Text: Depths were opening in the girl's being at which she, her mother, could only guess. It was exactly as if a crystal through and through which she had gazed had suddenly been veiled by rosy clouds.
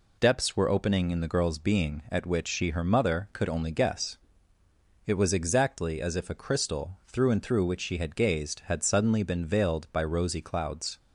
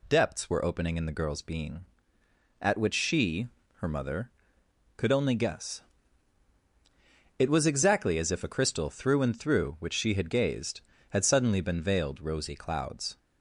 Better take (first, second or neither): first